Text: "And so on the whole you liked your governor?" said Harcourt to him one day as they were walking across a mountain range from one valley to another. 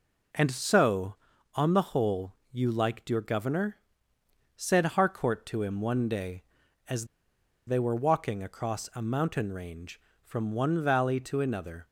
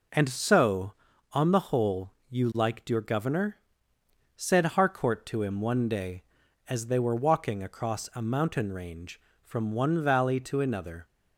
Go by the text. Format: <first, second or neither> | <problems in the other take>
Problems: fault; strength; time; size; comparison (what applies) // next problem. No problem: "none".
second | pauses between "whole" and "you"; slight; at 2.3 s; 0.18 s long; slight in the second // pauses between "as" and "they"; noticeable; at 7.0 s; 0.60 s long